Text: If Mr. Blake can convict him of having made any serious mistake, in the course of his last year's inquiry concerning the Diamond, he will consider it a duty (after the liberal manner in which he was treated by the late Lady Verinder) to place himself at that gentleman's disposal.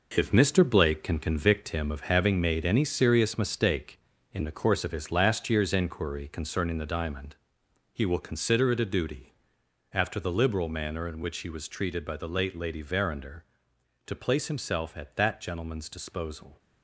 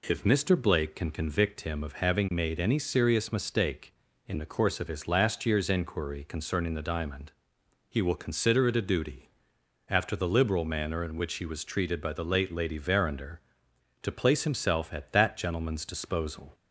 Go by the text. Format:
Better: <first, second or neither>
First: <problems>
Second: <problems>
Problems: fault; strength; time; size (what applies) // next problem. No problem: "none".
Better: second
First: gets quieter; strong; throughout; 9 dB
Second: none